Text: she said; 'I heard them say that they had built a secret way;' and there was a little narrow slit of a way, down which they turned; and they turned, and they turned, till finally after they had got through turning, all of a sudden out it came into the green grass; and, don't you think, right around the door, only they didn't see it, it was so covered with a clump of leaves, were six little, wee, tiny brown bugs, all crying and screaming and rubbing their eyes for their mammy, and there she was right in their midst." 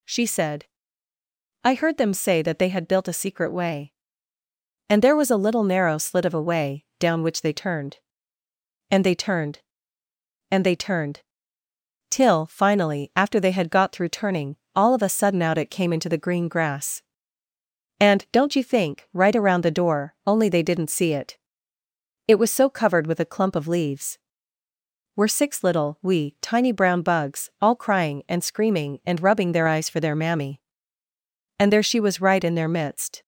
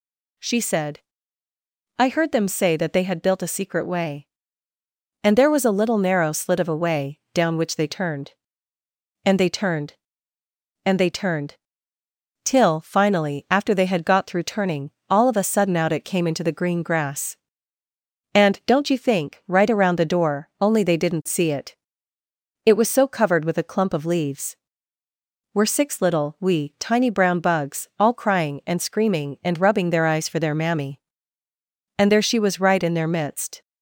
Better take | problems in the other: neither | none

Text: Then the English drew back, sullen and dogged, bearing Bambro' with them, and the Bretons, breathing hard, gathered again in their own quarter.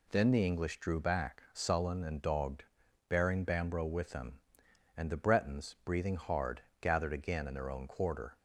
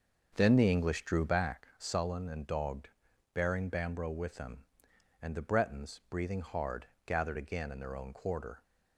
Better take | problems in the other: first | starts louder than the rest; until 1.6 s; 6.5 dB

